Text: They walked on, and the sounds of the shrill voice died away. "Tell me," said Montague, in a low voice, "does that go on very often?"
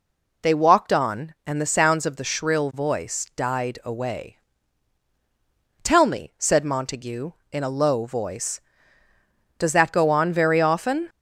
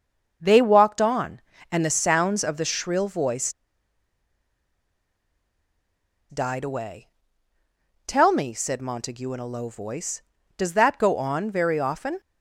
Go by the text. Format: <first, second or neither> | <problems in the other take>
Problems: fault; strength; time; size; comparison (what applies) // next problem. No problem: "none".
first | starts louder than the rest; until 1.7 s; 6.5 dB // pauses between "voice" and "died"; strong; at 3.5 s; 2.7 s long